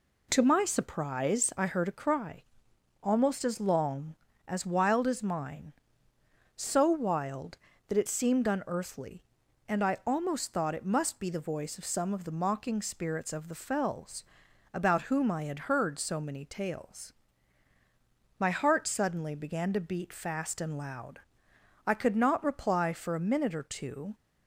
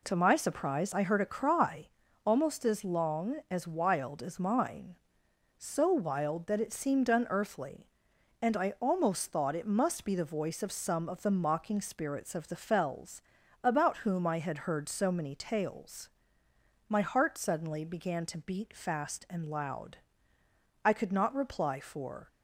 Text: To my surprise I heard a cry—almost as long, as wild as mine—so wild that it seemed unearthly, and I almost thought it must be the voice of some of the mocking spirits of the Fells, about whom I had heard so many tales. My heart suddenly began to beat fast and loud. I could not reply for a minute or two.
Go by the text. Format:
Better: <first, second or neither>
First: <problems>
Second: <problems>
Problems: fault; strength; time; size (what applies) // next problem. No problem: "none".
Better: first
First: none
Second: stops before "a minute or two"; at 22.2 s